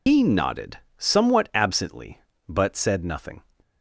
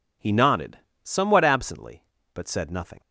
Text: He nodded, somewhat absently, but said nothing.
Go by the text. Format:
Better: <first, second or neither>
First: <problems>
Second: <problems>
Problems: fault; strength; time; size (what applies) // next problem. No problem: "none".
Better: second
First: loses the start of "He"; at 0.0 s; 70 ms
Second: none